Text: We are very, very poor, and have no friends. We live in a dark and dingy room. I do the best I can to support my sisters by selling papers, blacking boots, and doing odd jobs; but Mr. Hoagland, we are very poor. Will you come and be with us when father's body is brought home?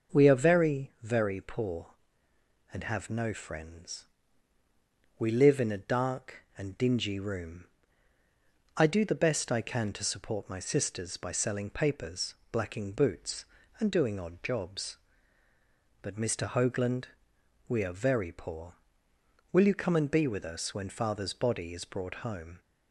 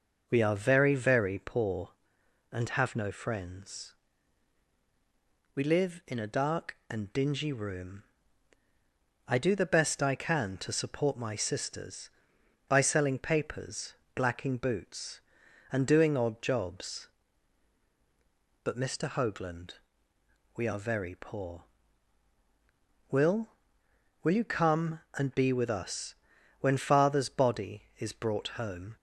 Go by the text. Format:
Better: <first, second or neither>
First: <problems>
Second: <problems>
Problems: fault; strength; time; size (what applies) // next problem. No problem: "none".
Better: first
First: none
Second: says "Will" twice; at 24.2 s // pauses between "us" and "when"; noticeable; at 26.1 s; 0.48 s long